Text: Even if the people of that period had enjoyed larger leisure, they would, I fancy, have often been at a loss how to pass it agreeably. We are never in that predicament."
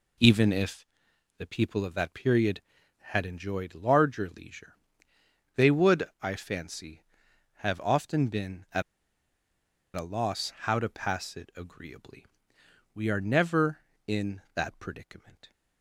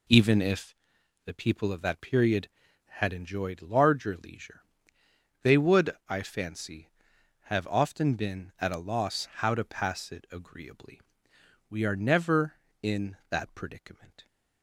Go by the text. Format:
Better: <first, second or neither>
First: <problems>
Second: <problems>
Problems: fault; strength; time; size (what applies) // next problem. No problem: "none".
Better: second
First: pauses between "if" and "the"; noticeable; at 0.8 s; 0.52 s long // pauses between "at" and "a"; at 8.8 s; 1.1 s long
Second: pauses between "if" and "the"; noticeable; at 0.7 s; 0.50 s long